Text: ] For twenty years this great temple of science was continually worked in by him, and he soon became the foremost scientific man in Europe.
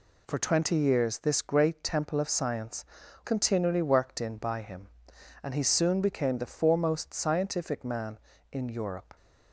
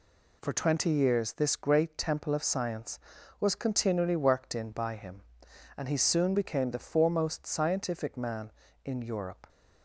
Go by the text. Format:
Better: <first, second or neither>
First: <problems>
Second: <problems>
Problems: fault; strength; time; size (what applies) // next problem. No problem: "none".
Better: second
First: skips "was"; at 3.0 s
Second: none